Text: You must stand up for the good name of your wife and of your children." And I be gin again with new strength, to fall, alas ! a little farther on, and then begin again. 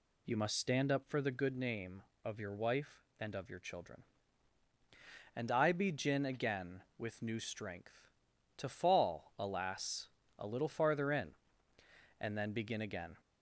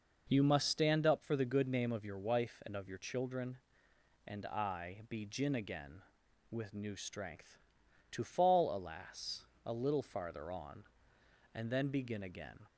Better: second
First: says "in" for "on"; at 11.1 s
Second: none

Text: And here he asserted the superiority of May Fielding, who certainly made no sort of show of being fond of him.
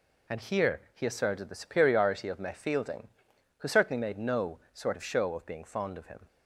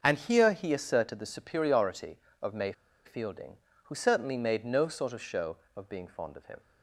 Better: first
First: none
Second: starts louder than the rest; until 1.0 s; 6.5 dB // pauses between "May" and "Fielding"; slight; at 2.7 s; 0.33 s long

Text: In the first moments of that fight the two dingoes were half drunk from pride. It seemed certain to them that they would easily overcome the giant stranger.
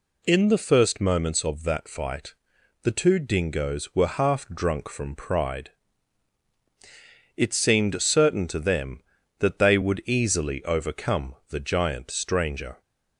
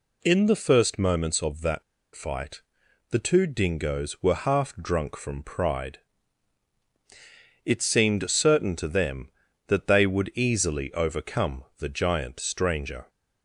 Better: first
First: pauses between "fight" and "the"; noticeable; at 2.3 s; 0.50 s long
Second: pauses between "that" and "fight"; slight; at 1.8 s; 0.32 s long // pauses between "fight" and "the"; noticeable; at 2.6 s; 0.50 s long

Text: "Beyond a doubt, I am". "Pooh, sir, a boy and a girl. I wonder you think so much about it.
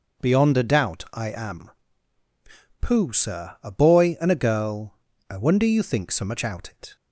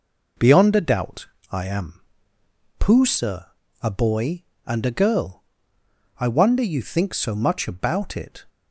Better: second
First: starts louder than the rest; noticeable; until 1.3 s; 6 dB // says "out" for "about"; at 6.4 s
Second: none

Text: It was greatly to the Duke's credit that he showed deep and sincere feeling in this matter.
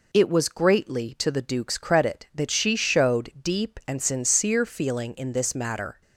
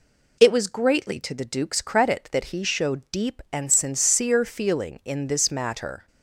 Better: second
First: says "she" for "he"; at 2.5 s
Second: none

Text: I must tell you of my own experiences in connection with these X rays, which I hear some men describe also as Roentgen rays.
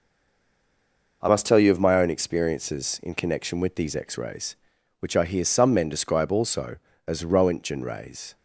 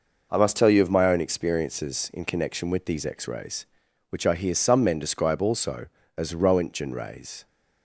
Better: second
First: stays silent before the first word; noticeable; until 1.2 s; 1.2 s long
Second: none

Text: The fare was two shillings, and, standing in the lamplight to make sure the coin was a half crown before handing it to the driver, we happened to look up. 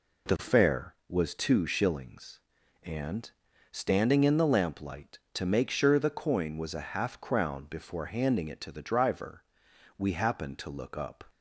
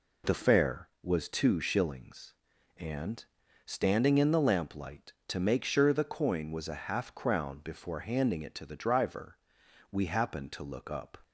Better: neither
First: none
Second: none

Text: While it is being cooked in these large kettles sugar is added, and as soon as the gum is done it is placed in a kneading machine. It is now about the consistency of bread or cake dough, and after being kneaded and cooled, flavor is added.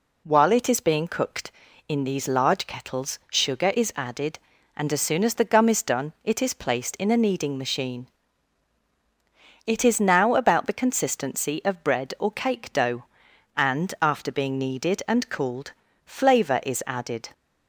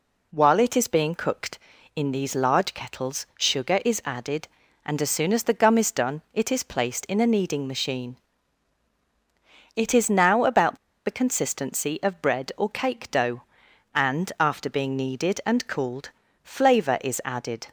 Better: first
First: none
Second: pauses between "about" and "the"; slight; at 10.7 s; 0.28 s long

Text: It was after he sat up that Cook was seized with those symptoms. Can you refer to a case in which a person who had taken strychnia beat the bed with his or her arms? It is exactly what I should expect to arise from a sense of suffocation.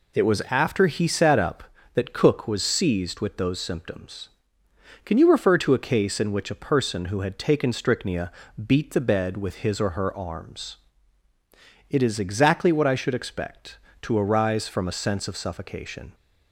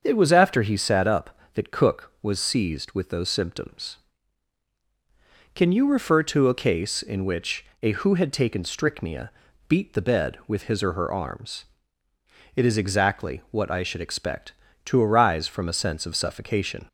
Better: first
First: pauses between "strychnia" and "beat"; slight; at 8.3 s; 0.34 s long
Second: starts louder than the rest; until 1.0 s; 6.5 dB // pauses between "which" and "a"; slight; at 7.6 s; 0.18 s long // skips "person"; at 7.9 s // pauses between "strychnia" and "beat"; at 9.2 s; 0.38 s long

